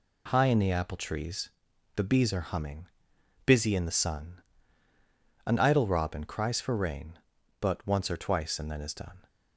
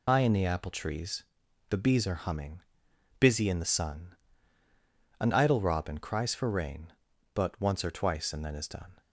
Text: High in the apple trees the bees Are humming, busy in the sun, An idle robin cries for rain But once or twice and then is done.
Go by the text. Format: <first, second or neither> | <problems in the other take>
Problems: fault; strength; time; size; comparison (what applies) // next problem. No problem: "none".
first | loses the start of "High"; at 0.0 s; 80 ms // pauses between "trees" and "the"; at 1.2 s; 0.44 s long; also in the first